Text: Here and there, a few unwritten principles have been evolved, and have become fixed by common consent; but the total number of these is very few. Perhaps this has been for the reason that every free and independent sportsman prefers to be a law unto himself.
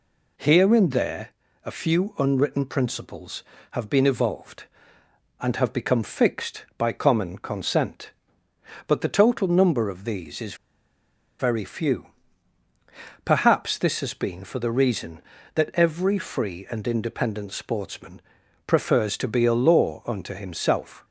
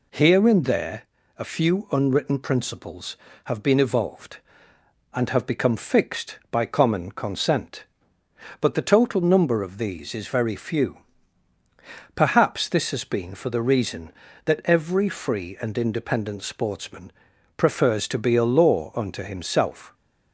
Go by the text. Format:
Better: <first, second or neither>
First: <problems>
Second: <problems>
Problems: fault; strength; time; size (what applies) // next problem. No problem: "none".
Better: second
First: pauses between "is" and "very"; noticeable; at 10.5 s; 0.85 s long // pauses between "sportsman" and "prefers"; noticeable; at 18.2 s; 0.46 s long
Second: pauses between "sportsman" and "prefers"; noticeable; at 17.1 s; 0.46 s long